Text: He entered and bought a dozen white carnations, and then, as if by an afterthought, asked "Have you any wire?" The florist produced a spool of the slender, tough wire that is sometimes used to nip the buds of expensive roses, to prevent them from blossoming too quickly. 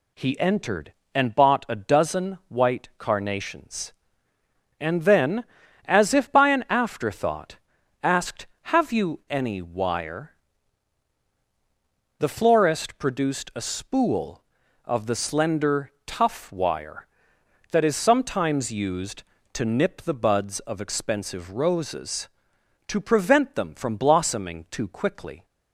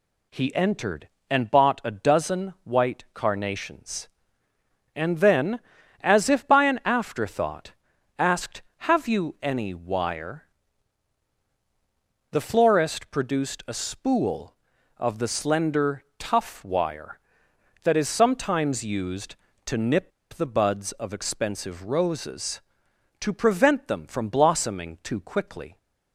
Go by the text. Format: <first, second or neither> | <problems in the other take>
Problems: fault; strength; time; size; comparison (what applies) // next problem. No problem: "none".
first | pauses between "nip" and "the"; slight; at 20.1 s; 0.22 s long